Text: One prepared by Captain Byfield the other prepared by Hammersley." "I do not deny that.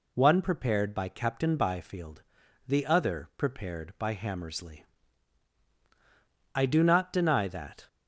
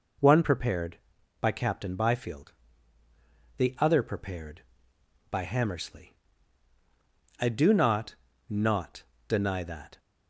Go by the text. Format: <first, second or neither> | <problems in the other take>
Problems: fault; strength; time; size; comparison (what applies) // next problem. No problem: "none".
first | pauses between "Byfield" and "the"; at 2.5 s; 1.0 s long; noticeable in the first // says "not" twice; at 8.4 s